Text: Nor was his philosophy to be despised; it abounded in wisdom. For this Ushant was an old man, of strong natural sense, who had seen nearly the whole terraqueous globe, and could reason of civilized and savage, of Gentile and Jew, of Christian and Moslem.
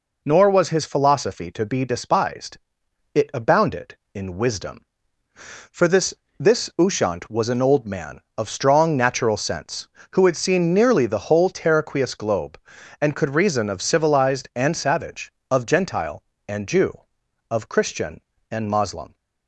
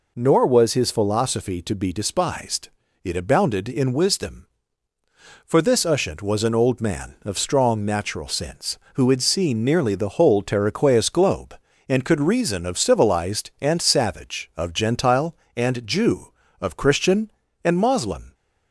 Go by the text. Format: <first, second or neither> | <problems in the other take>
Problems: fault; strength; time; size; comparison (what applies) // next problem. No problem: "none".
second | says "this" twice; at 6.3 s